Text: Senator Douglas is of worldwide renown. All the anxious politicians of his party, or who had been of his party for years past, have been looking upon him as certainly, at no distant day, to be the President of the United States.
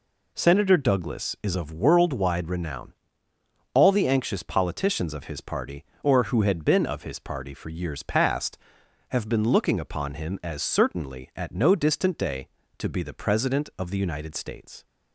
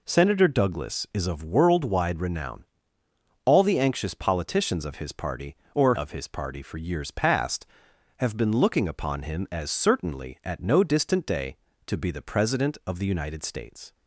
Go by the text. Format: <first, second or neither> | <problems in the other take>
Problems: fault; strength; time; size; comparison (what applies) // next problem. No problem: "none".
first | skips "who had been"; at 5.9 s